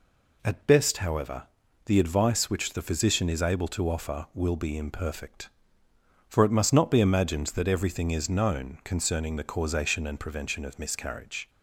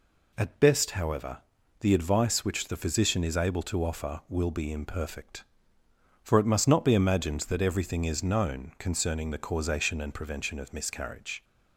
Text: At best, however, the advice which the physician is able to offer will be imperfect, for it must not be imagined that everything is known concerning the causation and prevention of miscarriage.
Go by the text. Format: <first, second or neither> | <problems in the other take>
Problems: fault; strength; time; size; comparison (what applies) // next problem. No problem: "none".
neither | none